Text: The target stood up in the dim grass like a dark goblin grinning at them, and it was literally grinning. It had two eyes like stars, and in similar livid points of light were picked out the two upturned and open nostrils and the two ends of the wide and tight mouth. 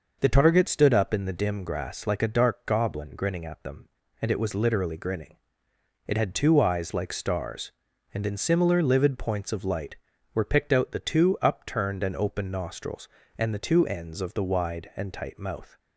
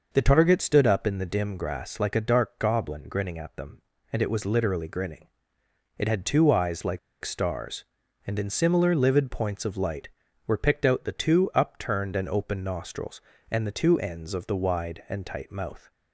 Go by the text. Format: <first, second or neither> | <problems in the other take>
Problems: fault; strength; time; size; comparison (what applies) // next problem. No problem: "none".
first | pauses between "like" and "stars"; slight; at 6.9 s; 0.24 s long